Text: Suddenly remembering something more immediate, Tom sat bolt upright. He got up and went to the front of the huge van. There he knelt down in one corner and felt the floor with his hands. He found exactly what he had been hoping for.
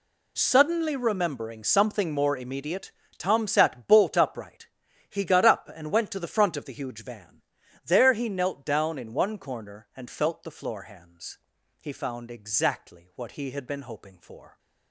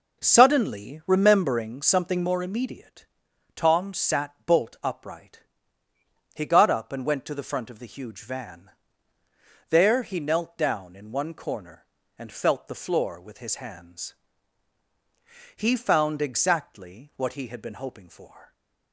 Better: second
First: skips "with his"; at 10.8 s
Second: none

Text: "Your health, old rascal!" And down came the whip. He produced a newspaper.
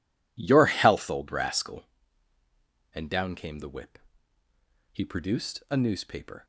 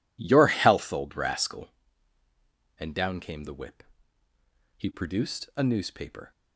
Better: neither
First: none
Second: none

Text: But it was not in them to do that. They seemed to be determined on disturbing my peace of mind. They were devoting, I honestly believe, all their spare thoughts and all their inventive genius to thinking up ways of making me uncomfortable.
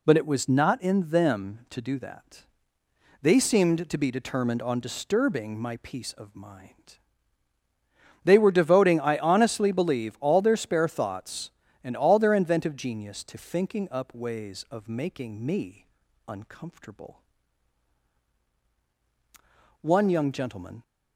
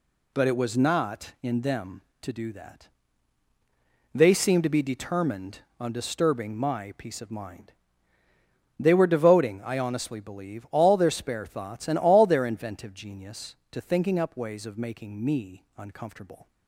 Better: second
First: pauses between "me" and "uncomfortable"; at 15.8 s; 0.42 s long // goes on to say "One young gentleman"; noticeable; from 19.8 s on; 1.0 s long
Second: none

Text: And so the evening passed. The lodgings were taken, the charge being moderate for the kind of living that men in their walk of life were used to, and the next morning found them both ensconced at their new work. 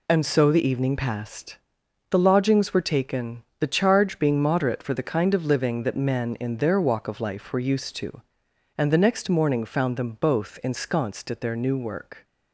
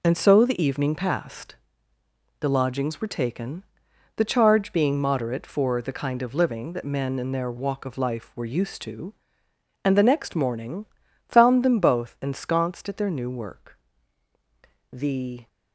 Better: first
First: none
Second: pauses between "morning" and "found"; at 10.8 s; 0.42 s long // goes on to say "The"; from 14.9 s on; 0.54 s long

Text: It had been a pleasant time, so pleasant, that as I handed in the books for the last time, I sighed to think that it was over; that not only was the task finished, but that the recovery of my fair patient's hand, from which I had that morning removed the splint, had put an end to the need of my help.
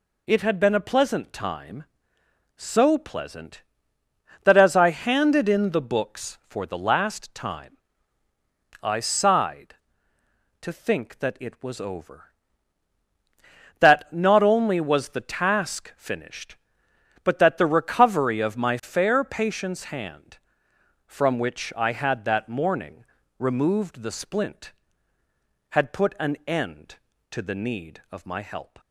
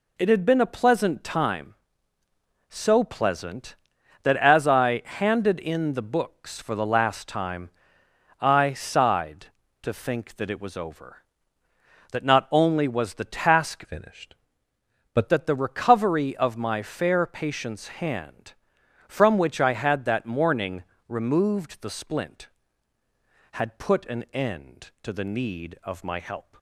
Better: first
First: pauses between "morning" and "removed"; slight; at 23.0 s; 0.34 s long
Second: changes voice from "finished" to "but"; from 13.8 to 15.2 s; 1.4 s long // pauses between "morning" and "removed"; slight; at 20.8 s; 0.24 s long

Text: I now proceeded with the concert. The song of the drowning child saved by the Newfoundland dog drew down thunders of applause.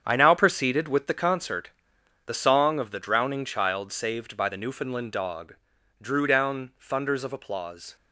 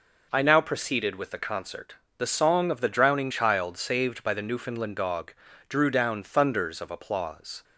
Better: second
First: gets quieter; strong; throughout; 10.5 dB // pauses between "dog" and "drew"; noticeable; at 5.5 s; 0.46 s long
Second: pauses between "dog" and "drew"; at 5.3 s; 0.38 s long

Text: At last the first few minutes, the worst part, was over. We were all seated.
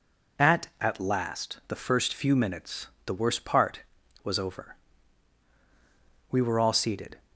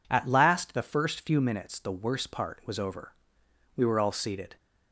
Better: second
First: says "At" twice; at 0.8 s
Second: none

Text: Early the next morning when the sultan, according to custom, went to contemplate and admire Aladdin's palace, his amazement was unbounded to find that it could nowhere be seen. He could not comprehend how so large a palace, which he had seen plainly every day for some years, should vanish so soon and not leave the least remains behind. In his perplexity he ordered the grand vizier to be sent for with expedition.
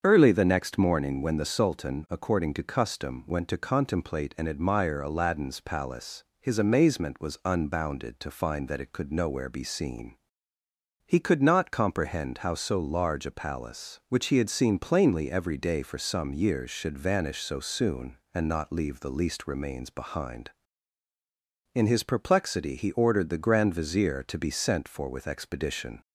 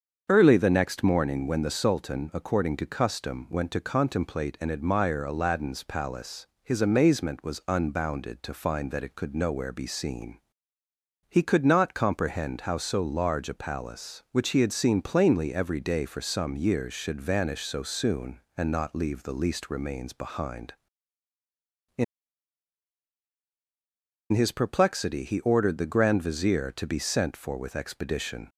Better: first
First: starts louder than the rest; until 1.0 s; 7 dB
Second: starts louder than the rest; until 1.3 s; 7 dB // pauses between "In" and "his"; strong; at 22.0 s; 2.2 s long

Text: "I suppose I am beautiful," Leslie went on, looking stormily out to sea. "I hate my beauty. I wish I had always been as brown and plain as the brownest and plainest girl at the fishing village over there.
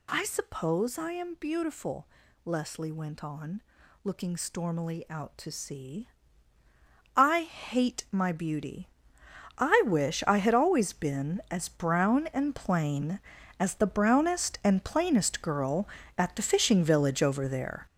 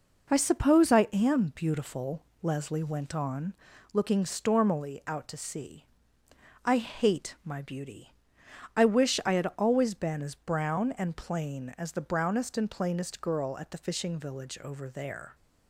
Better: second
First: gets louder; strong; throughout; 8.5 dB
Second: none

